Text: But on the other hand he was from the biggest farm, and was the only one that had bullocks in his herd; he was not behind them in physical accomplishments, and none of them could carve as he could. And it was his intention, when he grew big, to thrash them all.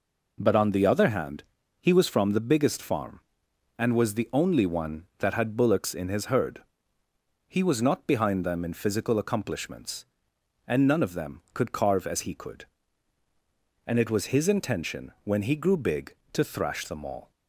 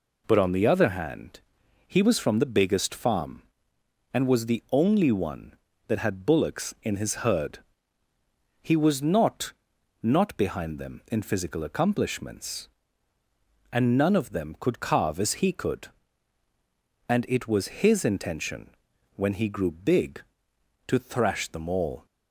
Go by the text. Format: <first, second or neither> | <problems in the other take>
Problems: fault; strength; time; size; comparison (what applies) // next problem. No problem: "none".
first | pauses between "hand" and "he"; noticeable; at 1.4 s; 0.46 s long; also in the first // says "not" twice; at 10.0 s